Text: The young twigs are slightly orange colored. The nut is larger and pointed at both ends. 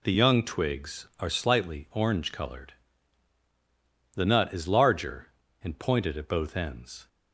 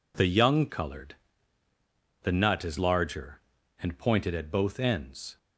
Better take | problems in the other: first | skips "twigs are slightly orange"; at 0.6 s

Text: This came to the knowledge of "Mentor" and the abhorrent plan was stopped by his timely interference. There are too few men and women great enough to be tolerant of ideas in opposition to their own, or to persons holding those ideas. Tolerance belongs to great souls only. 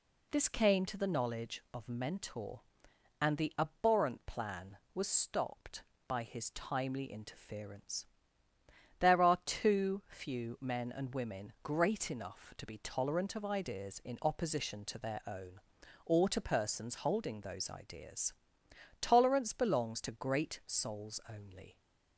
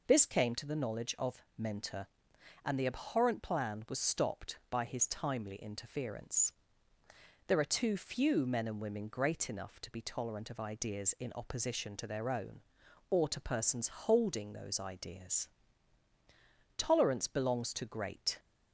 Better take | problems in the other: first | stops before "souls only"; at 18.3 s

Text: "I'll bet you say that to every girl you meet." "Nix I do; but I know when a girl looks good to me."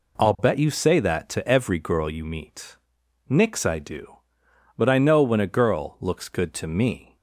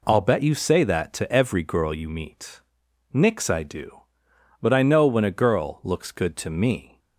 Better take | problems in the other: neither | none

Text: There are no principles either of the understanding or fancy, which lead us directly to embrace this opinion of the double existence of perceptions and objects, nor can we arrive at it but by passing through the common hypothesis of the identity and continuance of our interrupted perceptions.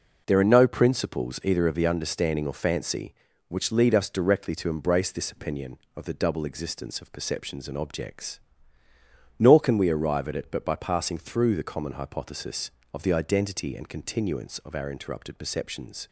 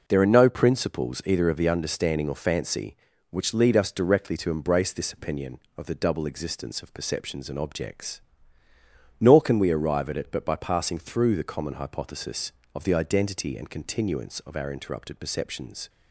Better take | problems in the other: neither | none

